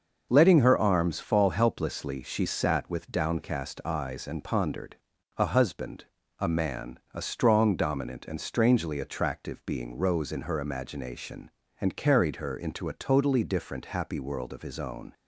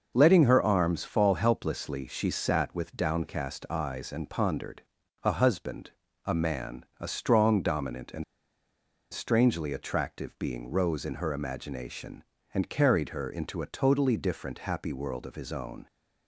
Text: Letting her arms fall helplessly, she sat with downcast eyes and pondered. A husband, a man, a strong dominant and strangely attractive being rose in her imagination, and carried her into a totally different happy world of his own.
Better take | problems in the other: first | starts louder than the rest; noticeable; until 1.1 s; 6 dB; noticeable in the first // pauses between "and" and "strangely"; noticeable; at 8.2 s; 0.88 s long

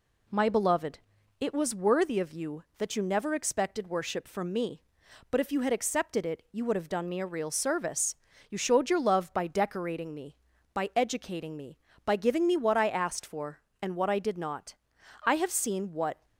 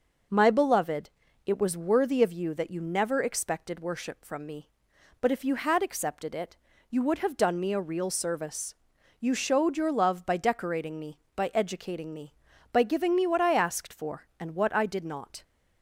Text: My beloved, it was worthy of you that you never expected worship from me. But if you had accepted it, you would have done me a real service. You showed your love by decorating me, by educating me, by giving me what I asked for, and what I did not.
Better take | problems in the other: second | goes on to say "I have seen what"; noticeable; from 15.2 s on; 1.0 s long

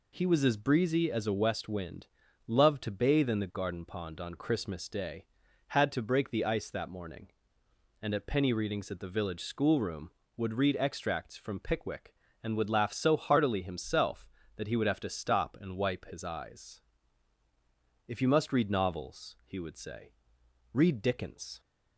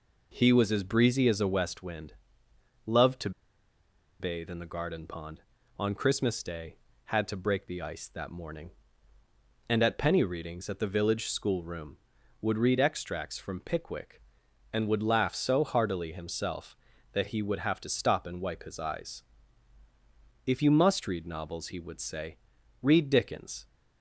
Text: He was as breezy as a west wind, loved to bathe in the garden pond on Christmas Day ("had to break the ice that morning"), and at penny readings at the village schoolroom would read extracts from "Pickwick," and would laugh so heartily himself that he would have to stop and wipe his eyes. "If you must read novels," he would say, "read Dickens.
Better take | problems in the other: first | pauses between "to" and "bathe"; noticeable; at 3.3 s; 0.89 s long

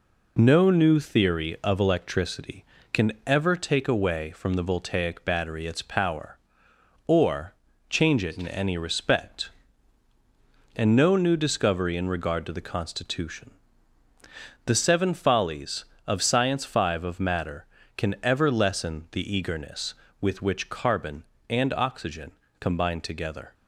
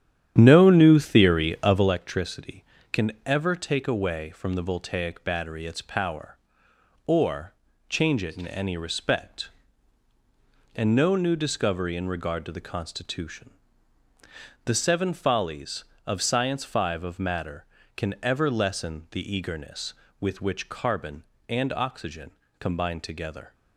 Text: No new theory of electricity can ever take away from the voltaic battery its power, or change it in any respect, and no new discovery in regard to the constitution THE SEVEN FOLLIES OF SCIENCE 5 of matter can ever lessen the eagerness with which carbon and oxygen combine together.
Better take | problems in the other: first | starts louder than the rest; strong; until 2.0 s; 10 dB // pauses between "or" and "change"; slight; at 7.5 s; 0.34 s long; slight in the first // pauses between "constitution" and "THE"; at 13.4 s; 1.1 s long; also in the first // pauses between "oxygen" and "combine"; slight; at 22.2 s; 0.30 s long; slight in the first

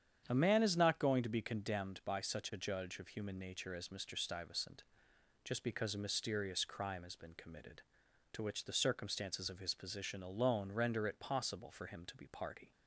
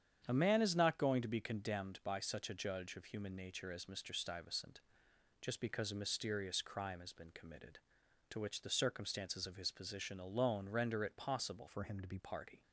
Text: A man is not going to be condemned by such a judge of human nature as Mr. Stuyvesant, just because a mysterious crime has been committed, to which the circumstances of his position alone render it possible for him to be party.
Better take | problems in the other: first | starts louder than the rest; strong; until 1.2 s; 8.5 dB; strong in the first // changes voice from "for" to "be"; from 11.6 to 12.1 s; 0.5 s long

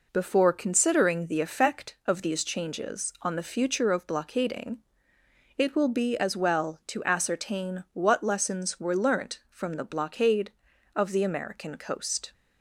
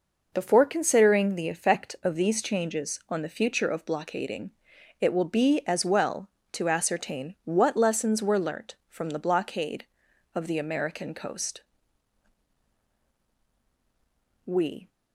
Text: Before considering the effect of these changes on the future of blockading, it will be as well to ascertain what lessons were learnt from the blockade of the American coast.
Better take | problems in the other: first | goes on to say "We"; slight; from 14.4 s on; 0.42 s long

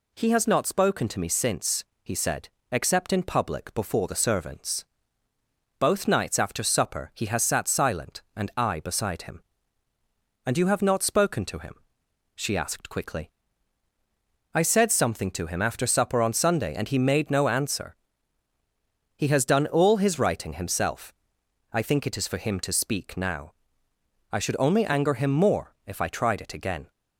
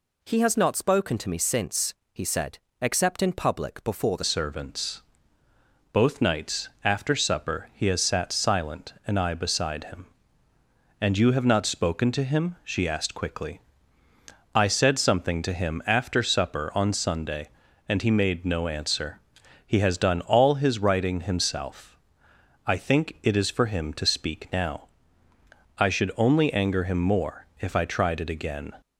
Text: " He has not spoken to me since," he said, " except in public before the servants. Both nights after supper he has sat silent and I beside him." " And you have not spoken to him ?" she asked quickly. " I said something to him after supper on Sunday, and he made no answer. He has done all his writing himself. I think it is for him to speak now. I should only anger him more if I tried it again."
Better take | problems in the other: first | changes voice at "servants"; from 4.2 s on; 24.5 s long // pauses between "nights" and "after"; slight; at 6.6 s; 0.16 s long

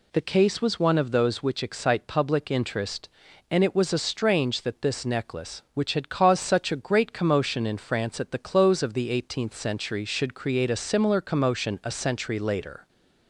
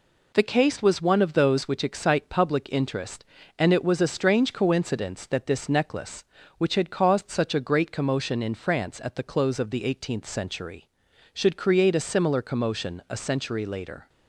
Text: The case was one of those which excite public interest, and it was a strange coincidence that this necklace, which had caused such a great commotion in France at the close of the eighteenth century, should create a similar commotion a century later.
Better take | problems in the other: second | skips "coincidence"; at 4.6 s

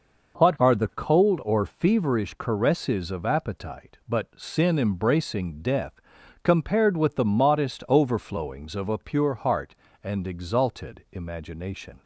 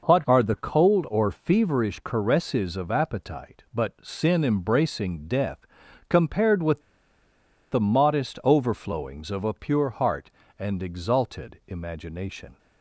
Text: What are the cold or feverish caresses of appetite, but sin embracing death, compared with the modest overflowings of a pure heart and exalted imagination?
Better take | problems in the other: first | pauses between "with" and "the"; noticeable; at 6.8 s; 0.89 s long

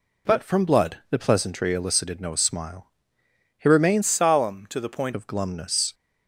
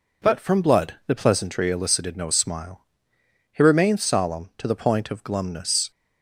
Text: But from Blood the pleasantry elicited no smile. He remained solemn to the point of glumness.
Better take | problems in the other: second | changes voice from "solemn" to "point"; from 4.0 to 5.1 s; 1.1 s long

